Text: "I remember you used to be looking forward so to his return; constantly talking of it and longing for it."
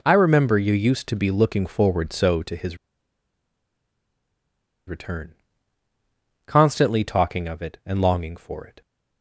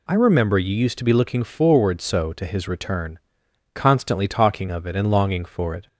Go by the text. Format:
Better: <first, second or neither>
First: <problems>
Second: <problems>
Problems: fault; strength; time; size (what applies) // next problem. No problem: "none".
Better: second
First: pauses between "his" and "return"; strong; at 2.7 s; 2.1 s long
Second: none